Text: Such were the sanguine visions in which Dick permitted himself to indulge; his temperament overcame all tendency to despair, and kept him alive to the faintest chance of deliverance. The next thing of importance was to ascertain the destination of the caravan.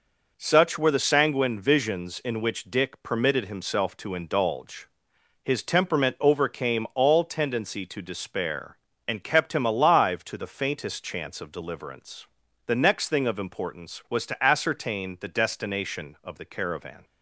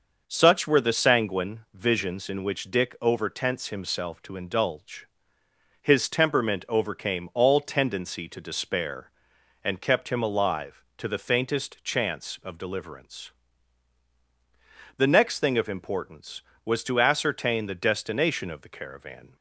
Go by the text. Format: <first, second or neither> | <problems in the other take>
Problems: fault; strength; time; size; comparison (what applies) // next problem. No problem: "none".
first | starts louder than the rest; until 1.2 s; 6 dB // says "overtense" for "permitted"; at 2.9 s